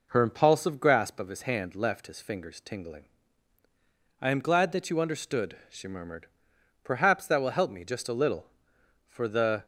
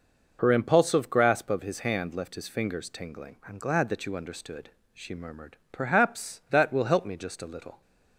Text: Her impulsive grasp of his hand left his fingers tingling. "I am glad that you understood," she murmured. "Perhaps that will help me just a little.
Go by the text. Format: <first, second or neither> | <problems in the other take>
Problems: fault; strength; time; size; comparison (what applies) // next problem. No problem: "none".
second | goes on to say "For the"; from 9.0 s on; 0.58 s long